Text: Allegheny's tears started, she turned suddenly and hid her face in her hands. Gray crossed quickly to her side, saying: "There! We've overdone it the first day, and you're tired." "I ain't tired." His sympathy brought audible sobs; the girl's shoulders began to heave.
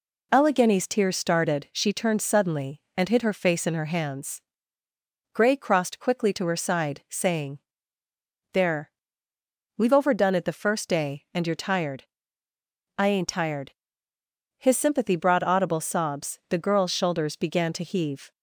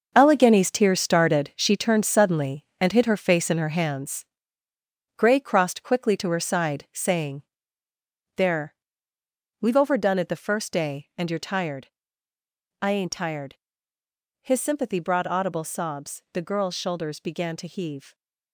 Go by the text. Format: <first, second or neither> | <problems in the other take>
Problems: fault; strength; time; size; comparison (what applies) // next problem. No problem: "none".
first | gets quieter; strong; throughout; 9 dB